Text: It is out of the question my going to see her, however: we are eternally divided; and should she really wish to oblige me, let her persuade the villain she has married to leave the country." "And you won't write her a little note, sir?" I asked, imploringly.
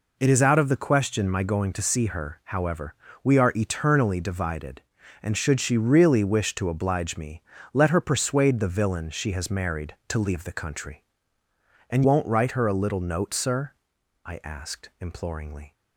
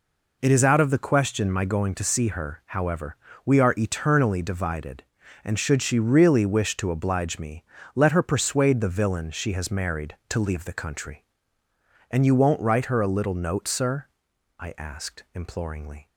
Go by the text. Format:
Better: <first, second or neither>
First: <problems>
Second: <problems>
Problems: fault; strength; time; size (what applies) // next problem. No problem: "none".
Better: second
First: skips "you"; at 12.0 s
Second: none